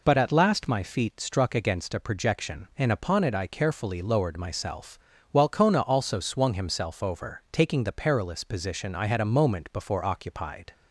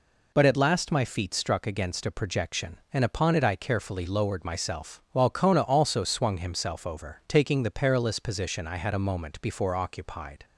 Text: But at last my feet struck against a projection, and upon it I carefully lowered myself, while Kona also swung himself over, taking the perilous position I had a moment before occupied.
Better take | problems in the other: neither | none

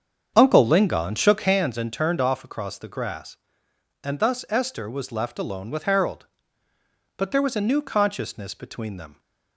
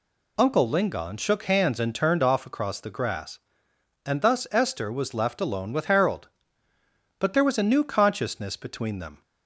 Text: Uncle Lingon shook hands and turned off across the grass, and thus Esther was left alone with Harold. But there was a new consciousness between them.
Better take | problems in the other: second | starts louder than the rest; strong; until 1.6 s; 7.5 dB

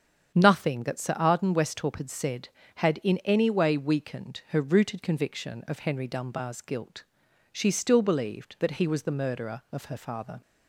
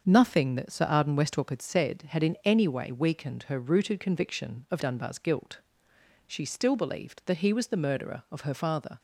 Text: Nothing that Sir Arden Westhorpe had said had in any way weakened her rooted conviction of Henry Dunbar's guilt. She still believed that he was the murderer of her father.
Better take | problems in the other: first | starts louder than the rest; until 1.0 s; 7 dB; strong in the first // skips "Henry"; at 4.8 s

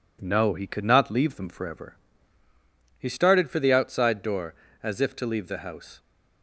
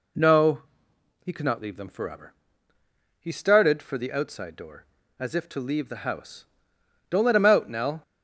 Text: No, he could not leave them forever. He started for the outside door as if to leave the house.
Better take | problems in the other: first | goes on to say "Don't let him out Nell"; noticeable; from 7.0 s on; 0.92 s long

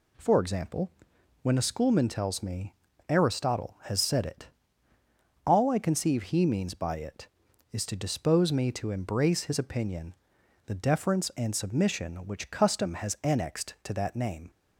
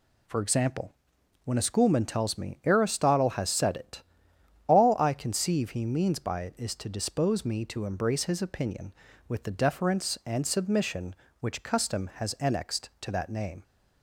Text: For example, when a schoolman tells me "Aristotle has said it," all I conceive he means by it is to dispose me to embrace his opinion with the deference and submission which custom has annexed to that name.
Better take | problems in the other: second | pauses between "me" and "Aristotle"; slight; at 2.7 s; 0.34 s long // skips "with"; at 10.4 s

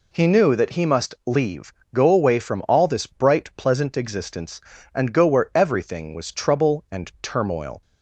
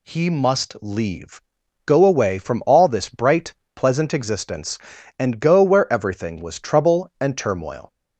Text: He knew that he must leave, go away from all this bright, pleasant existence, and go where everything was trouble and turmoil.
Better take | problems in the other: first | skips "knew that he"; at 0.2 s

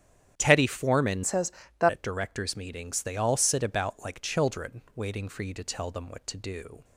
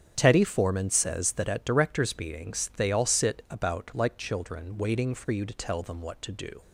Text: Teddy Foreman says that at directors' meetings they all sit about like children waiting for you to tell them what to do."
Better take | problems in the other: second | starts louder than the rest; strong; until 1.3 s; 10 dB; strong in the second // changes voice from "says" to "that"; from 1.2 to 1.8 s; 0.6 s long

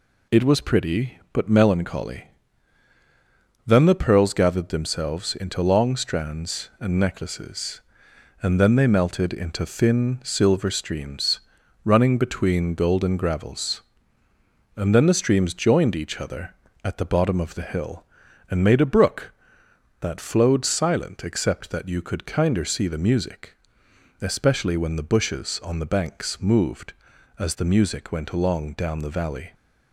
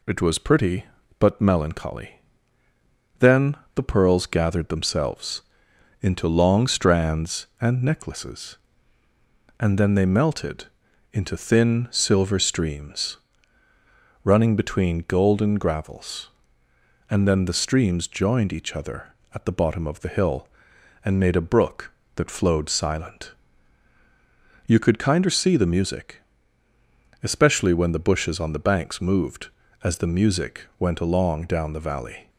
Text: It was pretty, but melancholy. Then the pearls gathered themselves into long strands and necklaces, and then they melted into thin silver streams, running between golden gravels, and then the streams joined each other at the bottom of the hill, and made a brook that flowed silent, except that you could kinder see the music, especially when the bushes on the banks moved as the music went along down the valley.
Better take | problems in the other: first | pauses between "Then" and "the"; slight; at 3.5 s; 0.19 s long // pauses between "themselves" and "into"; noticeable; at 5.4 s; 0.58 s long // pauses between "melted" and "into"; noticeable; at 10.6 s; 0.46 s long // skips "except that"; at 23.9 s // pauses between "music" and "went"; slight; at 30.6 s; 0.16 s long

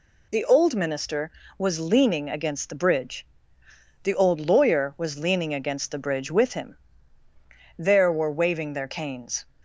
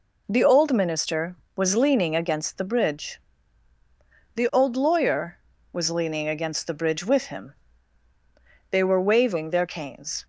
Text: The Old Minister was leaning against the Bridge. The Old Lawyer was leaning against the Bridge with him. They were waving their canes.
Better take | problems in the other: second | says "There" for "They"; at 7.7 s

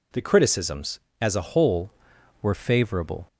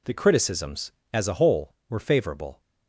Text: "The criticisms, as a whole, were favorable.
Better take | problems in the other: second | changes voice at "whole"; from 1.4 s on; 1.8 s long

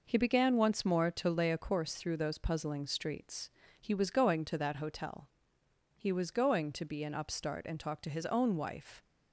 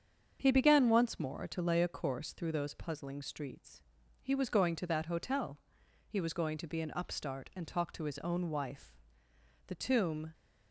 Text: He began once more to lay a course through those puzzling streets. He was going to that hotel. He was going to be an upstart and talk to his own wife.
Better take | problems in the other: first | starts louder than the rest; strong; until 1.4 s; 7 dB // goes on to say "The tomb"; noticeable; from 9.6 s on; 0.66 s long

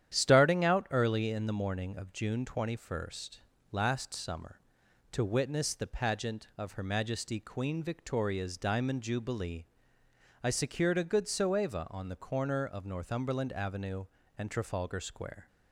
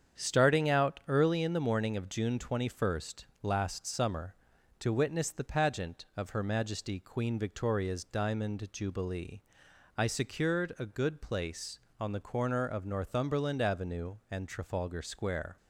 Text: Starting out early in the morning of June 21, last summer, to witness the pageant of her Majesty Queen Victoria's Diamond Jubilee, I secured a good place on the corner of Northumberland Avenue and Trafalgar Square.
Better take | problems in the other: second | starts louder than the rest; strong; until 1.1 s; 10 dB; strong in the second // says "soeva" for "place"; at 11.2 s

